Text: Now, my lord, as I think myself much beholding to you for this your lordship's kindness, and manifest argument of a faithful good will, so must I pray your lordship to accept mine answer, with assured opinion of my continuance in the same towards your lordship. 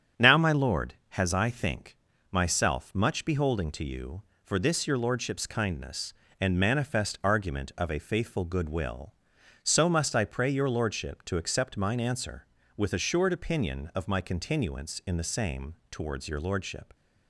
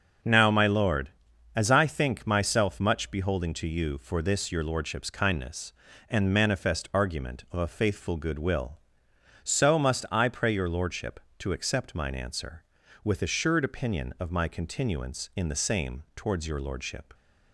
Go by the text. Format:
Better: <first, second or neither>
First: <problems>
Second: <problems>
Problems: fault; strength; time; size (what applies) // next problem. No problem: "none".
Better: second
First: starts louder than the rest; strong; until 1.3 s; 8.5 dB // says "has" for "as"; at 1.0 s // pauses between "think" and "myself"; slight; at 1.9 s; 0.34 s long // pauses between "same" and "towards"; slight; at 15.7 s; 0.18 s long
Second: starts louder than the rest; until 1.7 s; 6.5 dB